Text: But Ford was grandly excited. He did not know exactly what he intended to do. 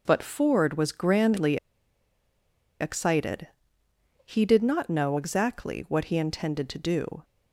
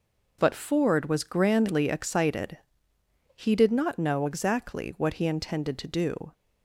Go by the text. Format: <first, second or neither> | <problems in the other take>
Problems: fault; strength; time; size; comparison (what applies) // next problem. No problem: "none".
second | pauses between "grandly" and "excited"; at 1.5 s; 1.2 s long